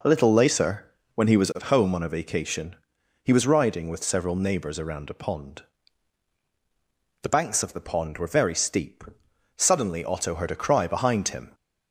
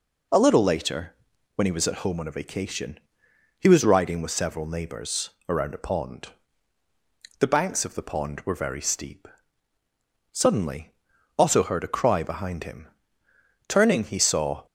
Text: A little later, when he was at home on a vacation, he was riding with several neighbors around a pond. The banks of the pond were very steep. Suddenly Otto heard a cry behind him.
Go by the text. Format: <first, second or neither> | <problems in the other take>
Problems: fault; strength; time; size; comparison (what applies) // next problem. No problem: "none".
first | pauses between "neighbors" and "around"; slight; at 5.2 s; 0.18 s long // pauses between "Suddenly" and "Otto"; noticeable; at 10.9 s; 0.46 s long // goes on to say "Turning he saw"; noticeable; from 13.6 s on; 0.98 s long